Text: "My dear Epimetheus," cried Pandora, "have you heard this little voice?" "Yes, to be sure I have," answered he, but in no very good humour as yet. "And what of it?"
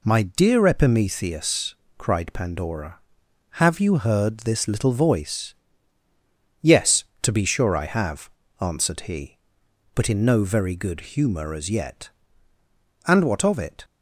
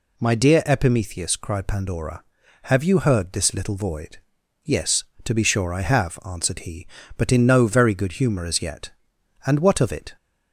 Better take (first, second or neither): first